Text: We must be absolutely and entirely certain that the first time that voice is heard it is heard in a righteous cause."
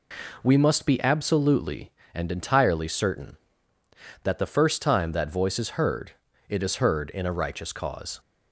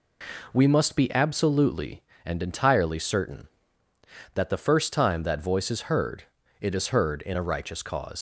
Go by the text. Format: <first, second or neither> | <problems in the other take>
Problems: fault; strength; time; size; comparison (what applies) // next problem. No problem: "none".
first | pauses between "heard" and "it"; slight; at 6.2 s; 0.36 s long; slight in the first // leaves "cause" unfinished; at 8.1 s; 90 ms